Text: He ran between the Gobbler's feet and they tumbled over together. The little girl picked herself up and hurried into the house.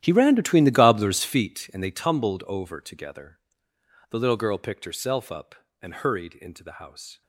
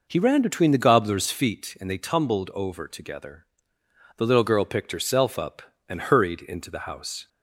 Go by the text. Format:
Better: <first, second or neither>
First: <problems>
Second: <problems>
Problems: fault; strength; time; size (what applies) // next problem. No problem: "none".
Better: second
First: gets quieter; strong; throughout; 18 dB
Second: none